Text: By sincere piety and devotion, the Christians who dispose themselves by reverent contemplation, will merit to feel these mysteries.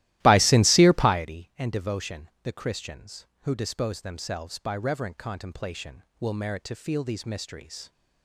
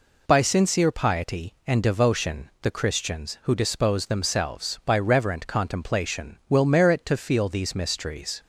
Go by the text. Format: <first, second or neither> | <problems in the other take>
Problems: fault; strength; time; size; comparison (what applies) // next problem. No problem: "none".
second | starts louder than the rest; strong; until 1.3 s; 15.5 dB